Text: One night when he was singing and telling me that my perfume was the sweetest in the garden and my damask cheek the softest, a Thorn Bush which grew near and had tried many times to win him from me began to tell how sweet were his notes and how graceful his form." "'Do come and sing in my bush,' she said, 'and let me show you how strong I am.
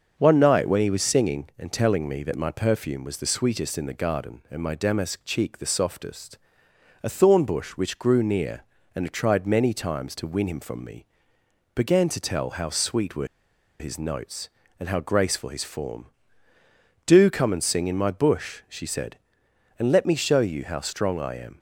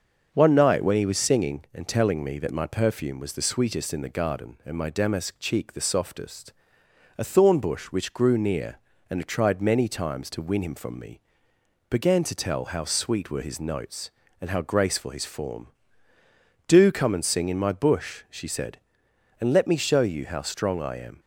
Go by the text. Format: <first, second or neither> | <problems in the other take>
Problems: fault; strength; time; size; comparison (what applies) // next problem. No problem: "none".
second | starts louder than the rest; until 1.1 s; 6.5 dB; also in the second // pauses between "me" and "began"; noticeable; at 11.0 s; 0.70 s long; noticeable in the second // pauses between "were" and "his"; noticeable; at 13.2 s; 0.53 s long